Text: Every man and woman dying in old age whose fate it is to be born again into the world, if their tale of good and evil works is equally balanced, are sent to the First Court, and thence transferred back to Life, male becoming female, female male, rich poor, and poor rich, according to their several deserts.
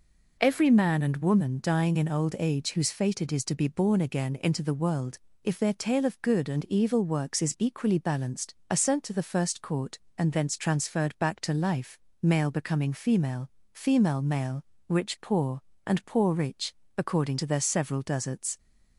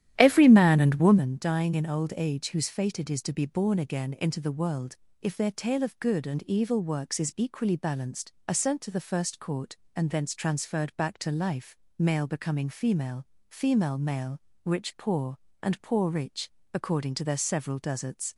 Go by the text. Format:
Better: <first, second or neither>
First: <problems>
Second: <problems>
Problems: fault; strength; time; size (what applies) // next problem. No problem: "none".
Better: first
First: none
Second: starts louder than the rest; strong; until 1.4 s; 11.5 dB